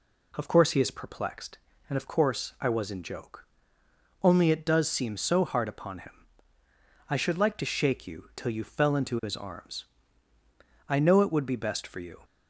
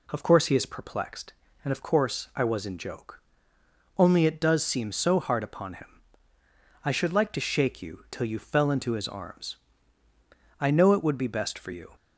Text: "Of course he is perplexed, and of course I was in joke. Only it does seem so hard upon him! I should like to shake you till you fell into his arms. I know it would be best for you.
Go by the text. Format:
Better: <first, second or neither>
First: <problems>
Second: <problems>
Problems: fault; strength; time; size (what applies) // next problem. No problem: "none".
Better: neither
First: none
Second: none